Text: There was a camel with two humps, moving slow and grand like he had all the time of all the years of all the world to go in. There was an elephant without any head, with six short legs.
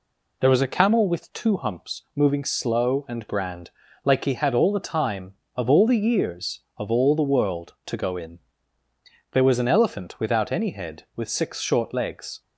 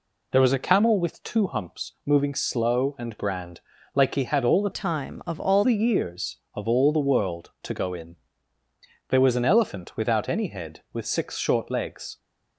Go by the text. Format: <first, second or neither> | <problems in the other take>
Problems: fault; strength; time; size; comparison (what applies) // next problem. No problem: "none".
first | pauses between "grand" and "like"; slight; at 3.5 s; 0.34 s long; slight in the first // changes voice from "time" to "all"; from 4.7 to 5.6 s; 0.9 s long